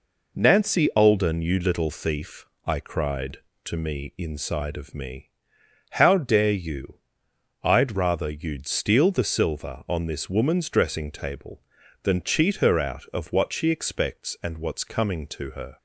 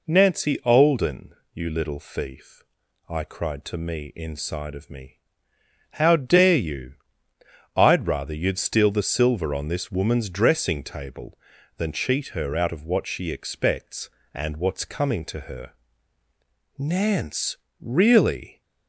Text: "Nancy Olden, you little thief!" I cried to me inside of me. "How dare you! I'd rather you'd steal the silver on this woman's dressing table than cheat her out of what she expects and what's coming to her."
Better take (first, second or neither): first